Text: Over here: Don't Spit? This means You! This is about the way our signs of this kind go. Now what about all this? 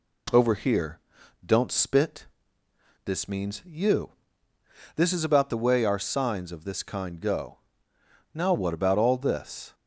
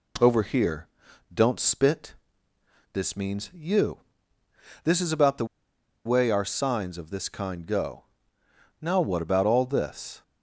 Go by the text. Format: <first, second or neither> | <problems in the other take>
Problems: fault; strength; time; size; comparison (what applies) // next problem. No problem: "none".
first | pauses between "the" and "way"; noticeable; at 5.4 s; 0.60 s long